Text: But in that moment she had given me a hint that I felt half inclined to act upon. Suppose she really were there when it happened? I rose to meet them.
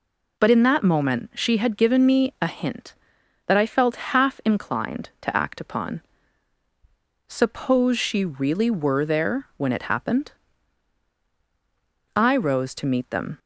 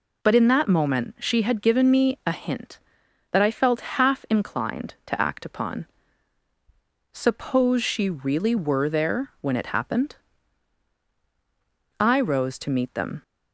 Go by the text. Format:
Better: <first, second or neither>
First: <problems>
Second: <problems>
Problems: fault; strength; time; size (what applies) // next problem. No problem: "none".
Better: neither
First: none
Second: none